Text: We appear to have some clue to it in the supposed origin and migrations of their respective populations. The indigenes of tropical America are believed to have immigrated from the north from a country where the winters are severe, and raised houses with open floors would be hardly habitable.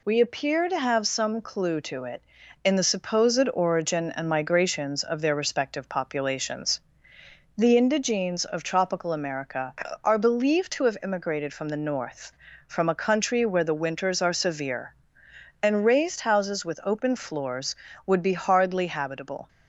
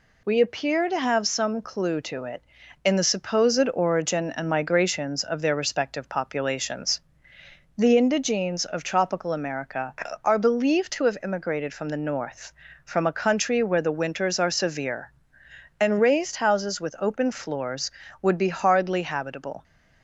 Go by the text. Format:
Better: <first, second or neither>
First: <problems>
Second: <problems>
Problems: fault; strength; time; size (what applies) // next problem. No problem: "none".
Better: neither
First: none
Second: none